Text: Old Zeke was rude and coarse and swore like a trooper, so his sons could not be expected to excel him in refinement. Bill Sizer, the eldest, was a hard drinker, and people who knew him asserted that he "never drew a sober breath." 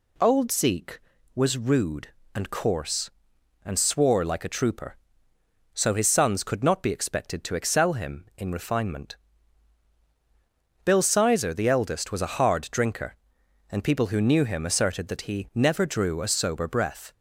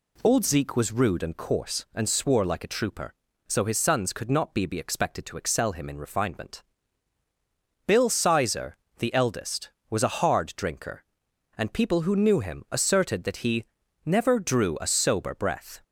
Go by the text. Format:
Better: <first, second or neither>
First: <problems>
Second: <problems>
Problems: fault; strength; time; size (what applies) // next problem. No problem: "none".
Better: first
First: none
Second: says "be" twice; at 4.6 s // pauses between "he" and "never"; at 13.6 s; 0.42 s long